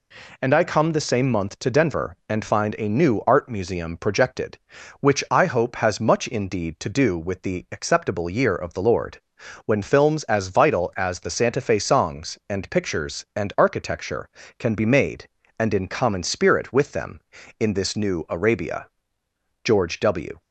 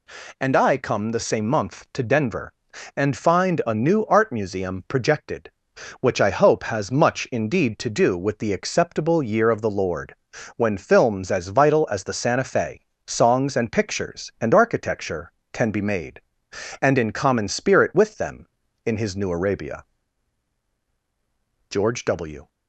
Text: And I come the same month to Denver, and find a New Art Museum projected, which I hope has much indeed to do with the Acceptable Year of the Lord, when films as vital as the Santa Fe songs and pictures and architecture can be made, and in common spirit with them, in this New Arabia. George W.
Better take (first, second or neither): first